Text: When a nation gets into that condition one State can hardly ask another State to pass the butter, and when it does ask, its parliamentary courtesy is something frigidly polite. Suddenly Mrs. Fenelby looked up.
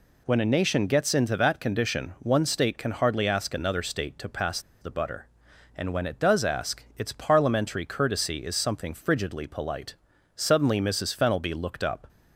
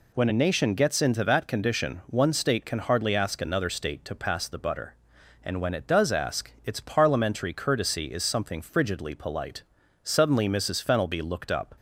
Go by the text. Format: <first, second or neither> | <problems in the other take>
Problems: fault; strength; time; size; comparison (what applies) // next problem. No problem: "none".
second | pauses between "pass" and "the"; slight; at 4.6 s; 0.19 s long